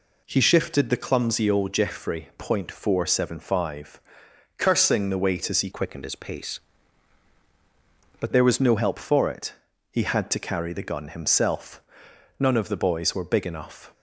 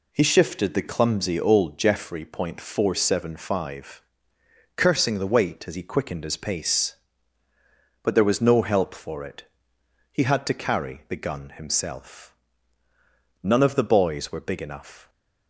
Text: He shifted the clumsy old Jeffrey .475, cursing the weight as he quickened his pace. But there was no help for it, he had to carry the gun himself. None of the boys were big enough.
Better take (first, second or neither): second